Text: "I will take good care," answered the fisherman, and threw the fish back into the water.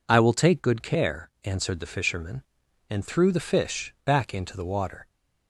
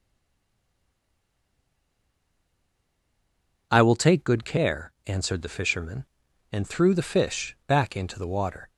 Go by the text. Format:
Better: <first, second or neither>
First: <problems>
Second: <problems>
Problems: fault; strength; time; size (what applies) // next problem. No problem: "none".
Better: first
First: none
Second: stays silent before the first word; strong; until 3.7 s; 3.7 s long